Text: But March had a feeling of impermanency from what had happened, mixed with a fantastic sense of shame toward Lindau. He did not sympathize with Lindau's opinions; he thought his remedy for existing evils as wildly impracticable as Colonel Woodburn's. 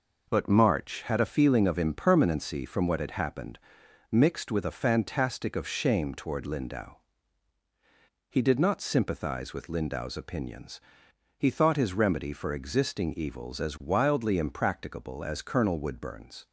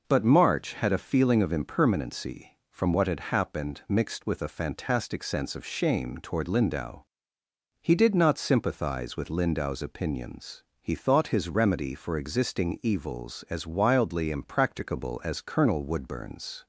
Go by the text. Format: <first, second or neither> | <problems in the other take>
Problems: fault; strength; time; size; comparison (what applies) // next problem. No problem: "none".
second | skips "sense"; at 5.5 s